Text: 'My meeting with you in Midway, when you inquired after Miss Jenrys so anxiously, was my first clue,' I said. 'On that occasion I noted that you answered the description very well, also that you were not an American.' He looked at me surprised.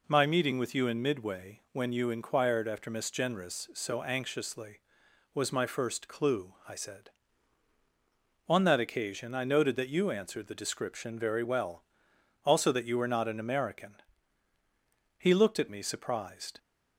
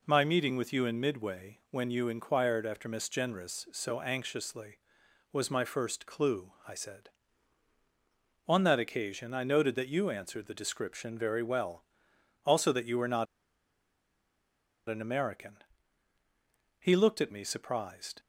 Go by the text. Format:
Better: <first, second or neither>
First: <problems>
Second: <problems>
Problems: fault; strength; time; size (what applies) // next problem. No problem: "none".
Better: first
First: none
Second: pauses between "not" and "an"; strong; at 13.2 s; 1.6 s long